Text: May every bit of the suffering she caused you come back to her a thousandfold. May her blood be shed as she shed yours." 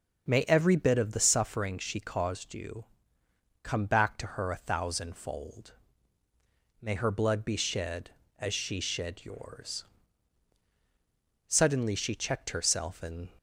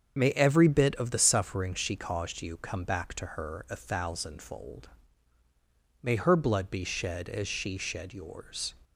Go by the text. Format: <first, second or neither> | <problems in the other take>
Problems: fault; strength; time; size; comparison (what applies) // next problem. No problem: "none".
second | starts louder than the rest; until 1.3 s; 6.5 dB; also in the second // pauses between "you" and "come"; noticeable; at 2.8 s; 0.80 s long // goes on to say "Suddenly she checked herself and"; strong; from 11.4 s on; 1.8 s long